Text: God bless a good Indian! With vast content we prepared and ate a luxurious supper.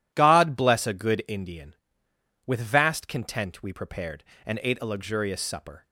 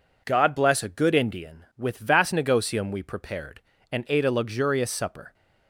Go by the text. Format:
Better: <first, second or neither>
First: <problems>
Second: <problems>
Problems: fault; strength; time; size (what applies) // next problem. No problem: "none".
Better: first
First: none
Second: says "negotium" for "content"; at 2.3 s